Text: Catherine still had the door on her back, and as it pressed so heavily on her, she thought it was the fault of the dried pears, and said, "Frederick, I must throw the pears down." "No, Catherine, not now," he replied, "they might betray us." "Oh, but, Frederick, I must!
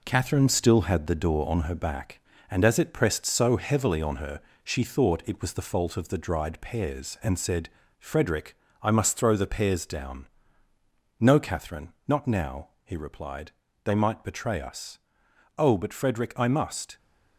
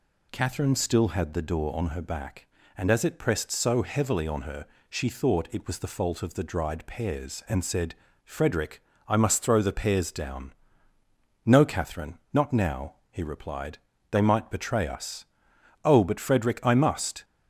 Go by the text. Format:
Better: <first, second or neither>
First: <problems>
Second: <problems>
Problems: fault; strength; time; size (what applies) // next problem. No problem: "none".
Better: second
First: gets quieter; noticeable; throughout; 5.5 dB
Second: none